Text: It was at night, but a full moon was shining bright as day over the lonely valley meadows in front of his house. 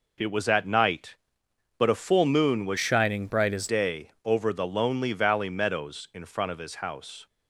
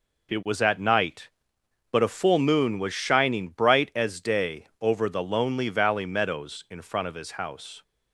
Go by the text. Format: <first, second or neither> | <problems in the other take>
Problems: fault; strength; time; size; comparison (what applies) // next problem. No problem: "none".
second | changes voice from "shining" to "as"; from 2.7 to 3.6 s; 0.9 s long